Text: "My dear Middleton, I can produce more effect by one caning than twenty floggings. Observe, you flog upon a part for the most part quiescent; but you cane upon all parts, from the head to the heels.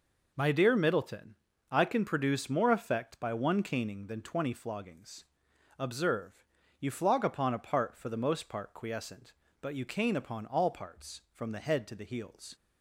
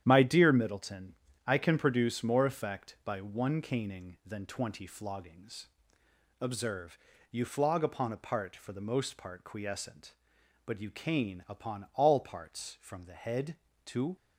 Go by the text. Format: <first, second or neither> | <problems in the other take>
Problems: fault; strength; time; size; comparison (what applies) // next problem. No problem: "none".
first | starts louder than the rest; strong; until 1.0 s; 10 dB // stops before "the heels"; at 14.1 s